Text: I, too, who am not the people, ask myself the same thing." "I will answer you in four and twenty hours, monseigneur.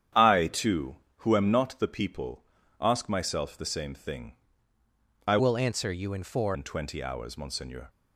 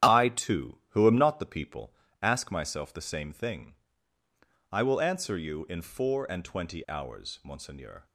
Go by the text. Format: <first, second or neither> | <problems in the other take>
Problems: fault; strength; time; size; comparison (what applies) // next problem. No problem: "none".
second | starts louder than the rest; strong; until 1.4 s; 9 dB; strong in the second // changes voice from "will" to "four"; from 5.3 to 6.5 s; 1.2 s long